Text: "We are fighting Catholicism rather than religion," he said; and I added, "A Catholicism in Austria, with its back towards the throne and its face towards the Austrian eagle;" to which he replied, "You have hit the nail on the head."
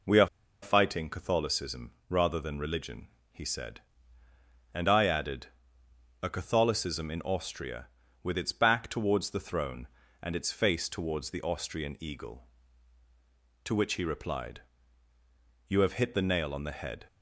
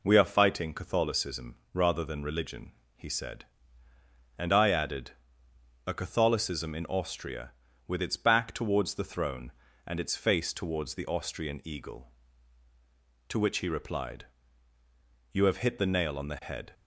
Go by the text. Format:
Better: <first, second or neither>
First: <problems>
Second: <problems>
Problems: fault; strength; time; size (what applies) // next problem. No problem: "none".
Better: second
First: pauses between "are" and "fighting"; slight; at 0.2 s; 0.35 s long // pauses between "Catholicism" and "rather"; slight; at 1.9 s; 0.16 s long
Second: pauses between "Catholicism" and "rather"; slight; at 1.5 s; 0.16 s long